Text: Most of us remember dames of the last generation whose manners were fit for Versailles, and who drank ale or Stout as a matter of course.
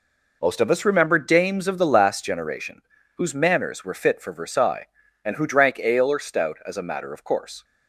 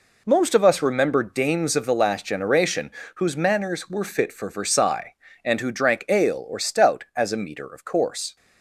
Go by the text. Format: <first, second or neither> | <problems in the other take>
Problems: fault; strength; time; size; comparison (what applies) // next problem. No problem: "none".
first | pauses between "generation" and "whose"; slight; at 2.8 s; 0.26 s long; slight in the first // says "meter" for "matter"; at 7.3 s